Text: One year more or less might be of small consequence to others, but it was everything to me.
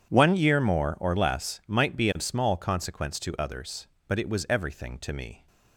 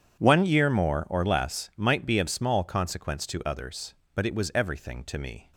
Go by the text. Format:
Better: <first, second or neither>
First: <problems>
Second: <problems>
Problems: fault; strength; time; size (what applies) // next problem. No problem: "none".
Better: neither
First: starts louder than the rest; strong; until 1.1 s; 9 dB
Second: starts louder than the rest; strong; until 1.2 s; 9 dB